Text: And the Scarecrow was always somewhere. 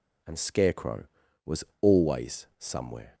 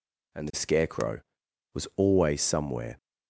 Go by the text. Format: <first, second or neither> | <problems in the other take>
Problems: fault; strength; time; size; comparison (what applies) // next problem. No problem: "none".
second | skips "the"; at 0.3 s // pauses between "was" and "always"; slight; at 1.6 s; 0.17 s long